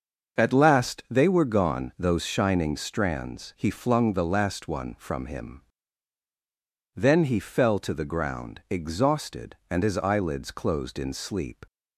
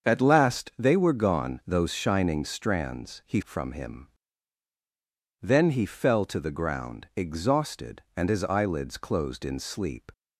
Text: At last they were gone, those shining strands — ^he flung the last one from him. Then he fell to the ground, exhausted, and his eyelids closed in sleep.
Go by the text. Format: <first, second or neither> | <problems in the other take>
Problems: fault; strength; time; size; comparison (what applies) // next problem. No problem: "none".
first | starts louder than the rest; until 1.1 s; 7 dB; also in the first // skips "flung the last one"; at 3.4 s